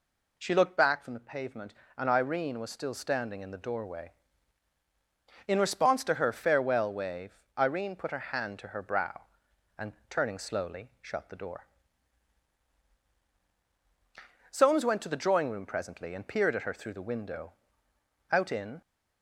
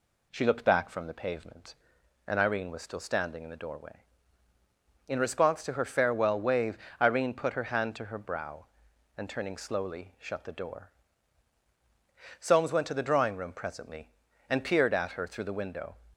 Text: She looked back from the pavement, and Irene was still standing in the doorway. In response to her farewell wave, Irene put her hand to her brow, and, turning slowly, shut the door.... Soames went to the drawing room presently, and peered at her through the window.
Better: second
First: goes on to say "Out in"; from 18.3 s on; 0.50 s long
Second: none

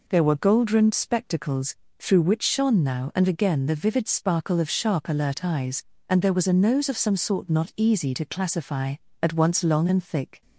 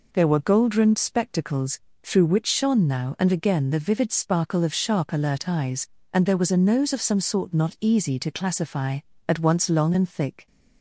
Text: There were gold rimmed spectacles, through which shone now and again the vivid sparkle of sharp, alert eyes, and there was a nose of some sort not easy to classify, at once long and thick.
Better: neither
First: none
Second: none

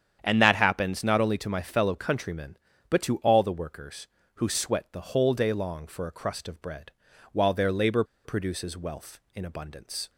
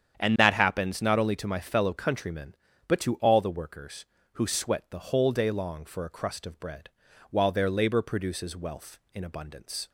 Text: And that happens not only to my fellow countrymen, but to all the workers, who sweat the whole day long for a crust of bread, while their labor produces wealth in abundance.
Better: second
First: starts louder than the rest; strong; until 1.2 s; 8.5 dB // pauses between "labor" and "produces"; slight; at 8.0 s; 0.22 s long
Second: starts louder than the rest; strong; until 1.2 s; 8.5 dB

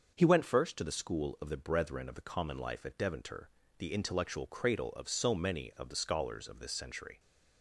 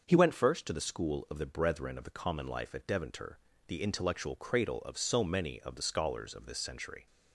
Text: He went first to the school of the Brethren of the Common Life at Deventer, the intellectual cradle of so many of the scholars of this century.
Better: neither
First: starts louder than the rest; until 1.1 s; 6.5 dB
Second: starts louder than the rest; until 1.0 s; 6.5 dB

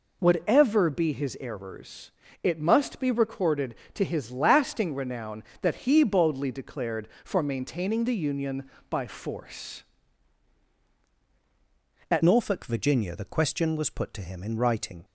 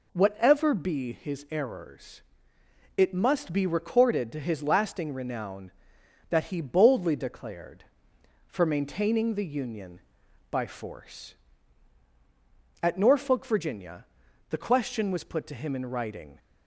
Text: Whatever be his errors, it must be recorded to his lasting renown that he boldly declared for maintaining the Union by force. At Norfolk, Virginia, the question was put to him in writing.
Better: second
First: changes voice at "Norfolk"; from 12.2 s on; 2.8 s long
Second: none

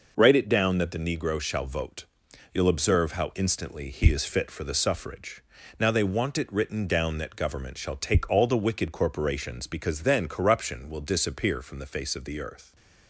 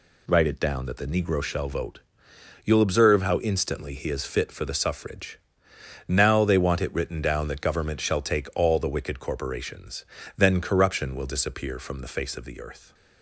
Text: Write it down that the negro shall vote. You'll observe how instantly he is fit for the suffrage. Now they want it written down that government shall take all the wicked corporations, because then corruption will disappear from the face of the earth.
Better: first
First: none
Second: skips "because"; at 10.1 s

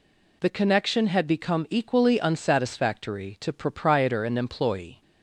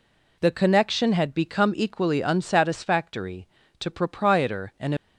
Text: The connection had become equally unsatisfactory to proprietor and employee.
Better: first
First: none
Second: stops before "employee"; at 4.9 s

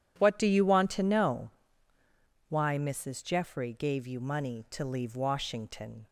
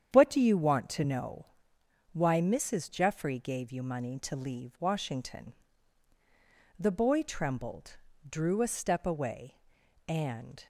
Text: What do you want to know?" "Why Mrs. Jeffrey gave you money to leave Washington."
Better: first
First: none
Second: starts louder than the rest; strong; until 1.1 s; 9 dB // goes on to say "The boy trembled drew a step away and"; strong; from 6.7 s on; 3.9 s long

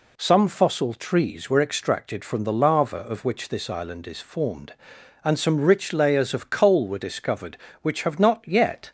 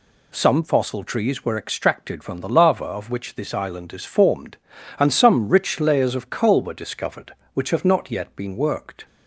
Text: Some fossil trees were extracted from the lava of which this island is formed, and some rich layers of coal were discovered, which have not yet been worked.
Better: second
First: stops before "been worked"; at 8.8 s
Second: none

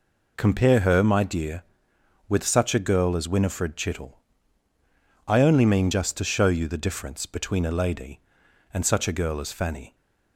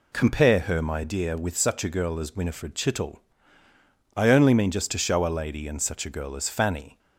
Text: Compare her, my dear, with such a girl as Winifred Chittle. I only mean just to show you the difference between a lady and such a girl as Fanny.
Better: first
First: none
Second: skips "you the difference between"; at 5.2 s

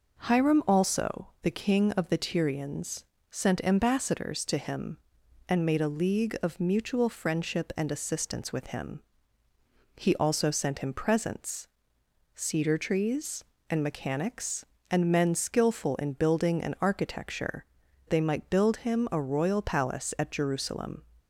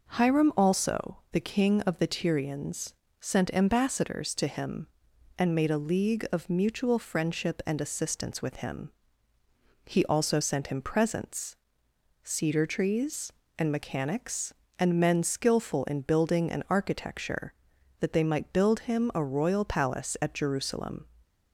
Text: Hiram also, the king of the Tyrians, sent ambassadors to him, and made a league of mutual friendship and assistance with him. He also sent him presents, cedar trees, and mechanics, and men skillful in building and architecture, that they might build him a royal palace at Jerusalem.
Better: second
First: skips "that"; at 17.8 s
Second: none

